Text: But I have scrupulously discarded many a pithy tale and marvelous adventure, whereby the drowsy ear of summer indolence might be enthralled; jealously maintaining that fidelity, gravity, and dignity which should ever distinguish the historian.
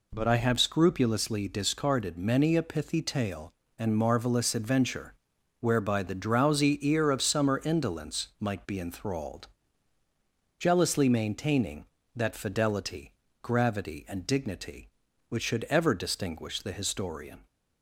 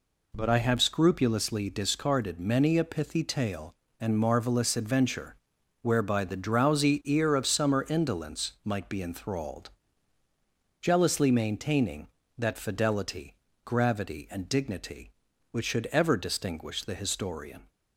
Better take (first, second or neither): neither